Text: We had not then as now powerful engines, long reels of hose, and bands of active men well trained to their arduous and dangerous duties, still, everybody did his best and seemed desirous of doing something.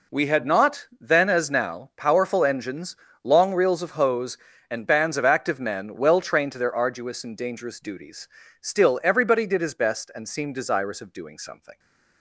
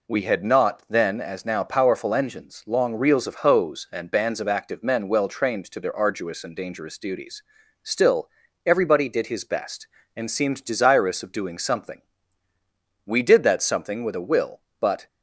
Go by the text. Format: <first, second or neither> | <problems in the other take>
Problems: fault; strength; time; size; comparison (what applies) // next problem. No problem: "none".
first | goes on to say "We did that something with a will but"; strong; from 13.0 s on; 2.0 s long